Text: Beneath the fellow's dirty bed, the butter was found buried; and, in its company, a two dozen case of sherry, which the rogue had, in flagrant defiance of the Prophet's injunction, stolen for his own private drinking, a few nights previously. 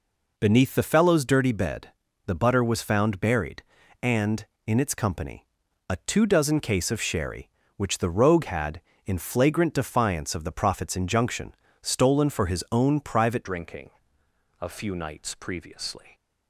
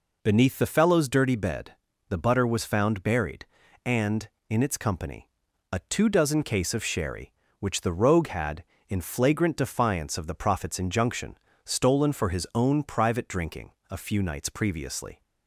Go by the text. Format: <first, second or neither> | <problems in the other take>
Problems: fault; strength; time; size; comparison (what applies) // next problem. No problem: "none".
second | changes voice at "drinking"; from 13.4 s on; 2.7 s long